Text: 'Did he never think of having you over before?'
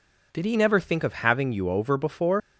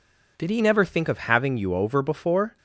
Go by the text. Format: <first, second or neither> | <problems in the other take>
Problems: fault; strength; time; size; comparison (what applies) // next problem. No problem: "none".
second | leaves "before" unfinished; at 2.4 s; 115 ms